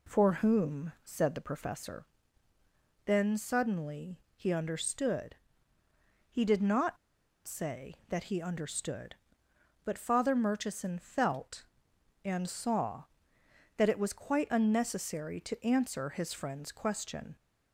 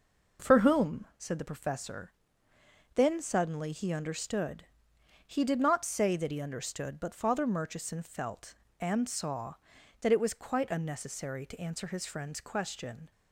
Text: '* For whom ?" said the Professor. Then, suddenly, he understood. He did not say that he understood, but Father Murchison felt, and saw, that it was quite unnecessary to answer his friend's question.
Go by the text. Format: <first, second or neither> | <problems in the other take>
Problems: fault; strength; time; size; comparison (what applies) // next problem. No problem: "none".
second | pauses between "not" and "say"; noticeable; at 6.9 s; 0.48 s long